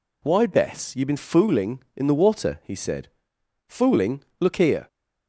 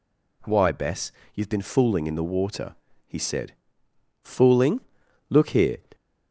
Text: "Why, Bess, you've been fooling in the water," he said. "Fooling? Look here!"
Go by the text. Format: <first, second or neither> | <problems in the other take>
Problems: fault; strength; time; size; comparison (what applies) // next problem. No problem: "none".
neither | none